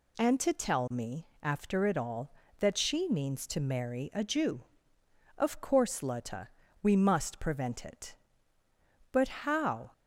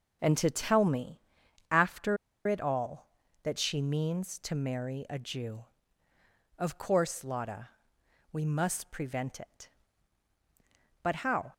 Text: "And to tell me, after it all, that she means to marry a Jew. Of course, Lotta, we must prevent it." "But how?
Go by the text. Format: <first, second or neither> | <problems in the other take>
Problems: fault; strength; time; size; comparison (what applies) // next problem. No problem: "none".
first | pauses between "after" and "it"; slight; at 2.1 s; 0.31 s long